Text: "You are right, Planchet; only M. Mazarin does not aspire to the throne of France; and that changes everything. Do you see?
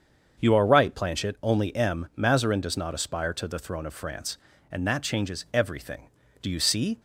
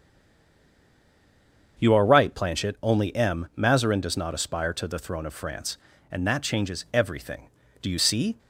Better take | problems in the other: first | stays silent before the first word; noticeable; until 1.7 s; 1.7 s long // starts louder than the rest; until 2.8 s; 7 dB; also in the first

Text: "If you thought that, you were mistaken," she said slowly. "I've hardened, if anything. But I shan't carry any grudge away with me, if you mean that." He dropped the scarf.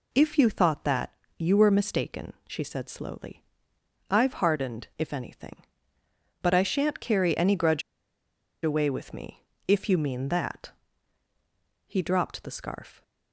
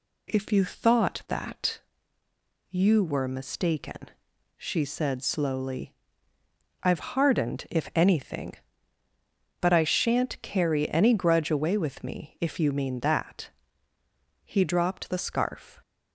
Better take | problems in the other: second | pauses between "grudge" and "away"; noticeable; at 7.8 s; 0.82 s long

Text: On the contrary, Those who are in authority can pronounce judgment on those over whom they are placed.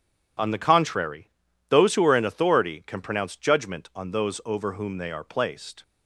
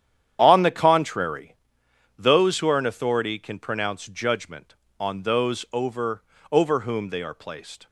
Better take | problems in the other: first | starts louder than the rest; strong; until 1.4 s; 9.5 dB // says "over" twice; at 6.5 s

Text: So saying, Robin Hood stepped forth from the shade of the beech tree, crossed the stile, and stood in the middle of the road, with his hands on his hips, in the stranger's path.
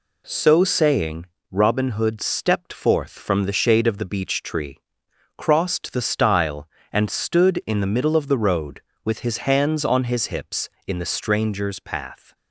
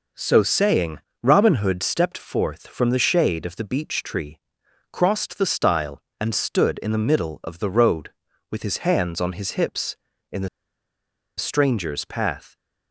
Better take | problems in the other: first | pauses between "the" and "stranger's"; noticeable; at 10.4 s; 0.90 s long

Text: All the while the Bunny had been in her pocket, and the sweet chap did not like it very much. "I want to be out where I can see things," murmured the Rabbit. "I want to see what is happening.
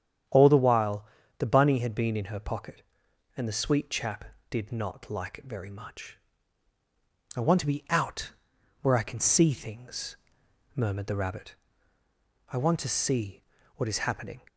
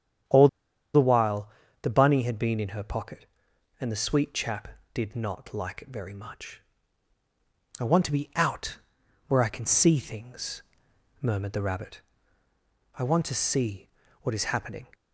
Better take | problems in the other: first | starts louder than the rest; strong; until 2.0 s; 9 dB; strong in the first // pauses between "All" and "the"; noticeable; at 0.4 s; 0.46 s long // pauses between "while" and "the"; slight; at 1.4 s; 0.34 s long; slight in the first // pauses between "out" and "where"; noticeable; at 8.7 s; 0.50 s long; noticeable in the first // pauses between "see" and "what"; slight; at 13.8 s; 0.32 s long; slight in the first

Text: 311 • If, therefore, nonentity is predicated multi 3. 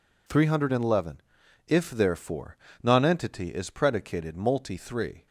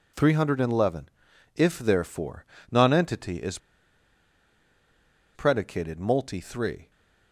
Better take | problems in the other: first | pauses between "is" and "predicated"; strong; at 3.5 s; 1.7 s long

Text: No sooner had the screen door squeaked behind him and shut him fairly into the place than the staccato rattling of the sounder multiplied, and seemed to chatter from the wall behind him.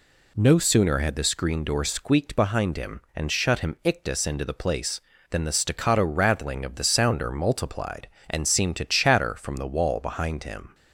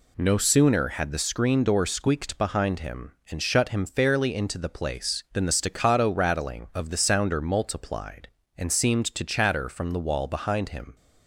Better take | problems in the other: second | says "ictus" for "fairly"; at 3.8 s

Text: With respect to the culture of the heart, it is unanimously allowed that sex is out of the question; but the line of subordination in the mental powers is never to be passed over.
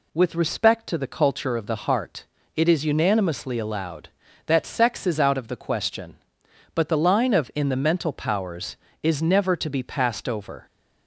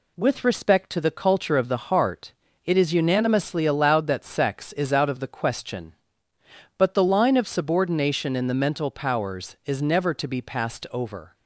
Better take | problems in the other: second | skips "subordination"; at 7.5 s

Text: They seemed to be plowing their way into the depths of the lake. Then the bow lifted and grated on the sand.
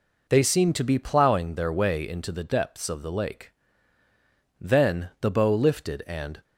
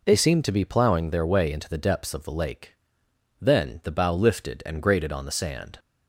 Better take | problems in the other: second | stops before "grated on the sand"; at 6.4 s

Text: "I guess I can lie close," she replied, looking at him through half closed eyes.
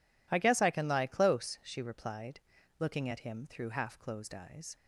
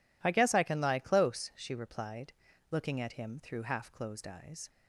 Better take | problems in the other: neither | none

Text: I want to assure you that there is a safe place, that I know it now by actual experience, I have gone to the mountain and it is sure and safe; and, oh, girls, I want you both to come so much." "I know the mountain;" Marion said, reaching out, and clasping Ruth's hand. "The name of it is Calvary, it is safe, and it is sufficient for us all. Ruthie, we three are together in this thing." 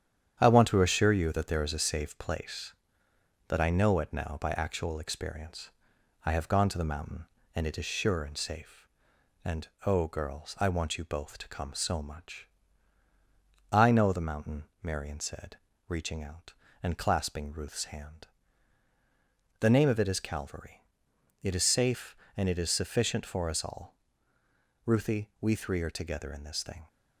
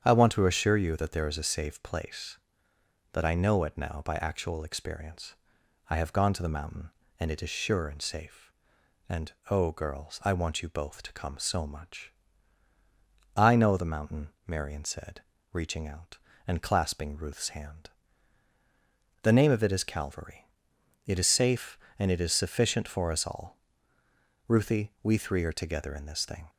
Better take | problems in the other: second | gets quieter; noticeable; throughout; 4.5 dB // starts louder than the rest; strong; until 1.4 s; 9 dB; strong in the second

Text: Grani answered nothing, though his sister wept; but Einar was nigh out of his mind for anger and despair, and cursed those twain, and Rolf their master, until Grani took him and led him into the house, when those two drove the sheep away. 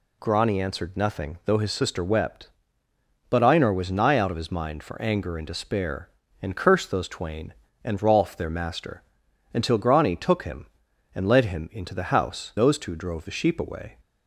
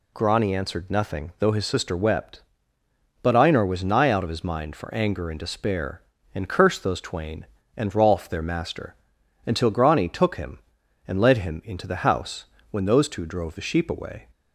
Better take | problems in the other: second | skips "when"; at 12.5 s

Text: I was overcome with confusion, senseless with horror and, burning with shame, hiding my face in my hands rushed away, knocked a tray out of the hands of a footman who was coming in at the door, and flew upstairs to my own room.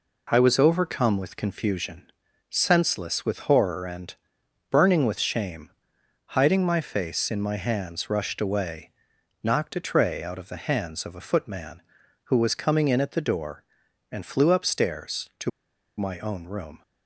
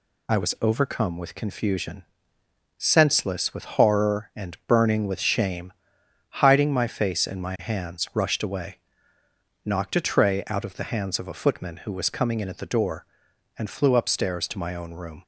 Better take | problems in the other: second | pauses between "to" and "my"; noticeable; at 15.5 s; 0.47 s long

